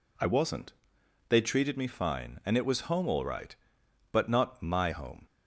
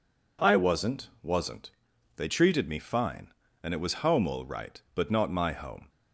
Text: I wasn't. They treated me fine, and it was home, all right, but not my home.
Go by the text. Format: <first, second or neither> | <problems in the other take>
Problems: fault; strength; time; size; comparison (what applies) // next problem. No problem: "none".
first | says "wasn't" twice; at 1.2 s